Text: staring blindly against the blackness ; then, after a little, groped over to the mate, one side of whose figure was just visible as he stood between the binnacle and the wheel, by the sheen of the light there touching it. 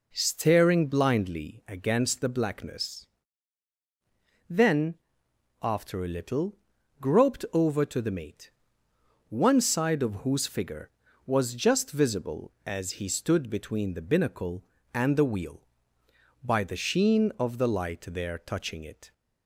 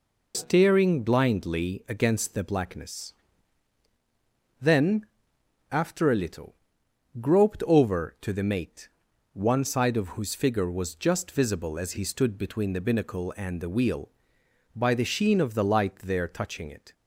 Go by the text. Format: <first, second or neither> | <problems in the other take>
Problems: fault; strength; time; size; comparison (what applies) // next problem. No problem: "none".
first | loses the start of "staring"; at 0.3 s; 30 ms